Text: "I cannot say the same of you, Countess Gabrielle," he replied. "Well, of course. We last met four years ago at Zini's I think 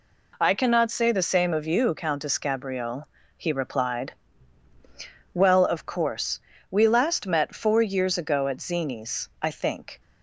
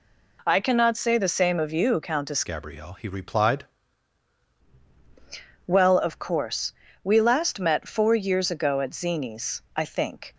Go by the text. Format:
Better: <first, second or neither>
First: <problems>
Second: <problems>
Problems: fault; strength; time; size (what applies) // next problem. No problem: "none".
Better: first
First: none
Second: changes voice from "Gabrielle" to "replied"; from 2.4 to 3.6 s; 1.2 s long